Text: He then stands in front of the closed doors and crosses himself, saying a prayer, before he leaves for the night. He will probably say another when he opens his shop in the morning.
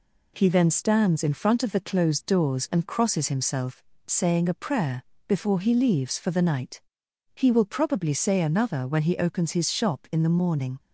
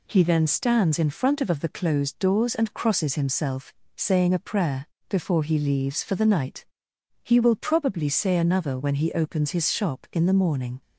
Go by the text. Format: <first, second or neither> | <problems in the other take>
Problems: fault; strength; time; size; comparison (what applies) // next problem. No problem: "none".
first | says "of" twice; at 1.5 s